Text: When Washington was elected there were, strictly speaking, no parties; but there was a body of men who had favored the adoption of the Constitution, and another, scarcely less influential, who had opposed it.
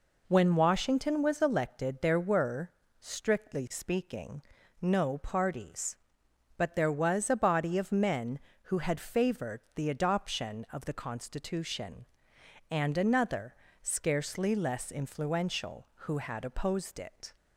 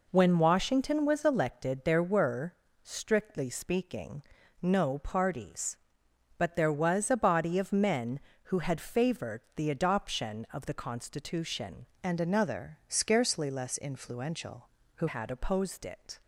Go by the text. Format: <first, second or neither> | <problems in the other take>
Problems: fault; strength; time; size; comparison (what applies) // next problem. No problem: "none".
first | changes voice from "and" to "who"; from 12.0 to 15.0 s; 3.0 s long